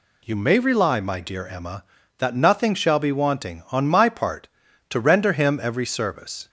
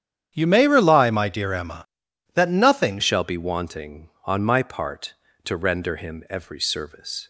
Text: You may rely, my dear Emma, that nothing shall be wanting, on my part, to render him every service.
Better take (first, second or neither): first